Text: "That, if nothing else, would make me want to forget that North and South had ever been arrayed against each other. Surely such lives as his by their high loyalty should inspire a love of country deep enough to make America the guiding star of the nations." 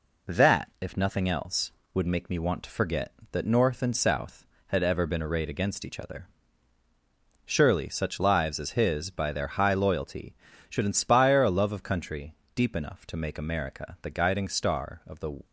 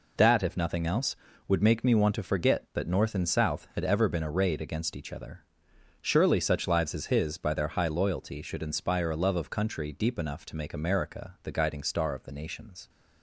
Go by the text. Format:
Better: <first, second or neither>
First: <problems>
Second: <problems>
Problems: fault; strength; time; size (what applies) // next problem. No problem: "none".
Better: second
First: pauses between "country" and "deep"; slight; at 12.3 s; 0.22 s long // stops before "nations"; at 15.4 s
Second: none